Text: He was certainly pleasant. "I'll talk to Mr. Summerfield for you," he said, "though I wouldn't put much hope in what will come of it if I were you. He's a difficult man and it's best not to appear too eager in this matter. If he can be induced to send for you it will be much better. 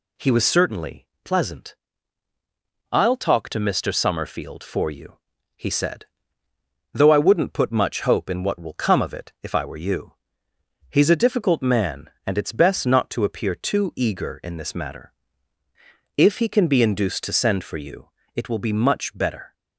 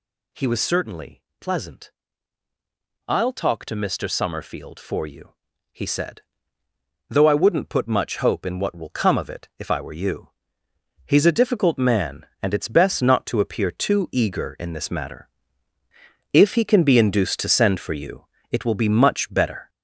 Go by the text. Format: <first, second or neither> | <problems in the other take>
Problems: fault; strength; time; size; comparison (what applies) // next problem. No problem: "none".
first | gets louder; throughout; 6.5 dB // pauses between "certainly" and "pleasant"; slight; at 1.2 s; 0.20 s long; slight in the first // pauses between "you" and "it"; slight; at 18.2 s; 0.26 s long; slight in the first